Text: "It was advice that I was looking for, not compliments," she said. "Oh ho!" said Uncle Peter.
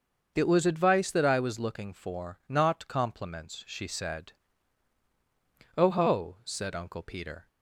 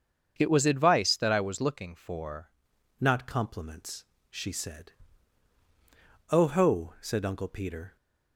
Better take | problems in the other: first | starts louder than the rest; until 1.3 s; 7 dB; also in the first // changes voice at "not"; from 2.9 s on; 5.0 s long

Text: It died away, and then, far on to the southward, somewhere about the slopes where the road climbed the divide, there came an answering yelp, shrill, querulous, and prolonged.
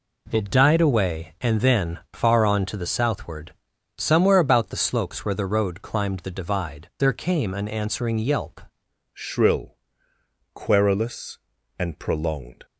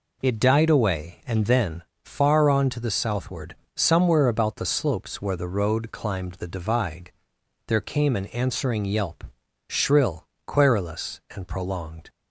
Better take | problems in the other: second | changes voice at "shrill"; from 9.1 s on; 3.5 s long

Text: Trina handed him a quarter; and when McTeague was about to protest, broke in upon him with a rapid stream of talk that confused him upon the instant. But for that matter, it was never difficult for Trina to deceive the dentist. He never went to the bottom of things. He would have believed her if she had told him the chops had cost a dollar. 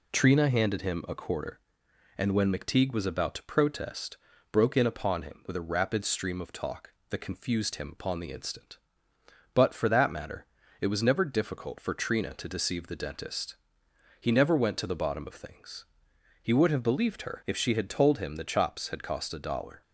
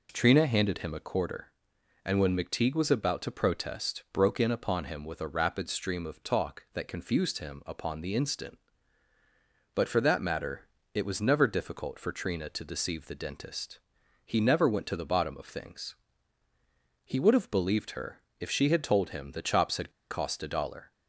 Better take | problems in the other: first | pauses between "her" and "if"; slight; at 18.2 s; 0.20 s long // pauses between "had" and "cost"; slight; at 19.9 s; 0.20 s long

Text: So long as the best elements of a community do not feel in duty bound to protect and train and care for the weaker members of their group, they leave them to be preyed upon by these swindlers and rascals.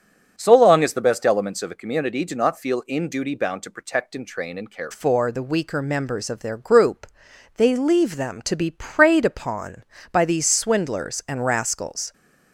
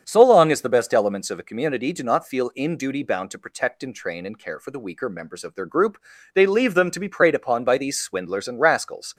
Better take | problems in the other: second | starts louder than the rest; strong; until 1.3 s; 8 dB; strong in the second // changes voice at "for"; from 4.9 s on; 7.2 s long

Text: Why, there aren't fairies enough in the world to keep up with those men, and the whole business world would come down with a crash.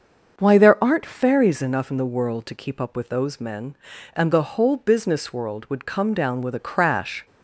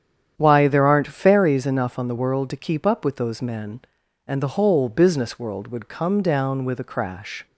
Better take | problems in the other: first | starts louder than the rest; strong; until 1.3 s; 9 dB; also in the first // says "on" for "in"; at 1.9 s

